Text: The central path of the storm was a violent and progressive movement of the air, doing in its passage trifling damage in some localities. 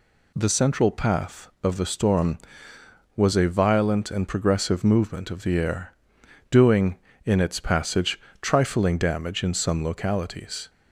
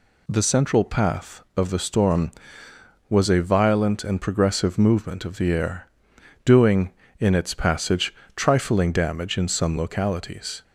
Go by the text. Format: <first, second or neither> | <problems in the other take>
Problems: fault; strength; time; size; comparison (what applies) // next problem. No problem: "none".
neither | pauses between "passage" and "trifling"; slight; the same in both